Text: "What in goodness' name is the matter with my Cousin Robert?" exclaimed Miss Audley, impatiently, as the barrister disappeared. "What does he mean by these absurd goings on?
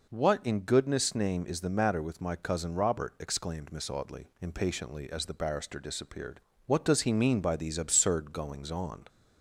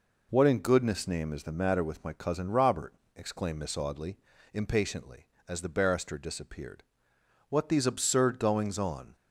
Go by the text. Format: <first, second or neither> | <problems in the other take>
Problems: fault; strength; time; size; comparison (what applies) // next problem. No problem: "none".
first | skips "does he mean by"; at 7.6 s